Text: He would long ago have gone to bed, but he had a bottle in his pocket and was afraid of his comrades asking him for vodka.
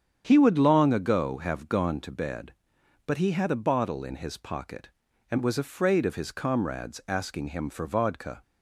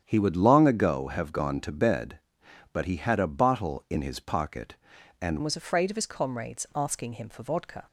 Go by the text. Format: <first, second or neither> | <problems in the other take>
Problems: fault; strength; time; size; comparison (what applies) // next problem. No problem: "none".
first | starts louder than the rest; strong; until 1.0 s; 9 dB; strong in the first // changes voice at "was"; from 5.4 s on; 2.4 s long